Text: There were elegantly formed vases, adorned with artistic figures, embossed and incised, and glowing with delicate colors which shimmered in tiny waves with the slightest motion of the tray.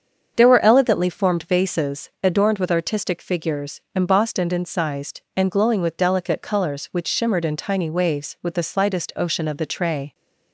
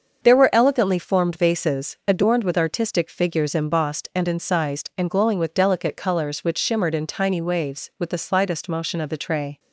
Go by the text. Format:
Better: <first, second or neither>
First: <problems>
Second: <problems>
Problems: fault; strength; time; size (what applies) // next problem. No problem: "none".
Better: second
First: starts louder than the rest; strong; until 1.3 s; 7 dB // says "ocean" for "motion"; at 9.1 s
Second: starts louder than the rest; until 1.2 s; 6.5 dB